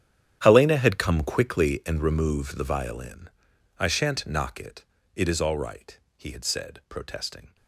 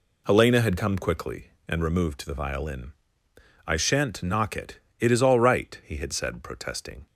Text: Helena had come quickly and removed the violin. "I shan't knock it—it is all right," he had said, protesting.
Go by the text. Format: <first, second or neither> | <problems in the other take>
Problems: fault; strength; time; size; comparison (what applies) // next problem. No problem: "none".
second | gets quieter; strong; throughout; 17.5 dB